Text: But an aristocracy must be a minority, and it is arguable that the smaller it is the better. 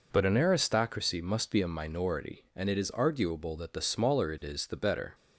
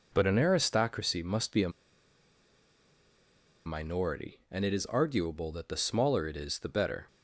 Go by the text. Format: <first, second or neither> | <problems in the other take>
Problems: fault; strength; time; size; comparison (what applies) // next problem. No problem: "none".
first | pauses between "a" and "minority"; strong; at 1.6 s; 1.9 s long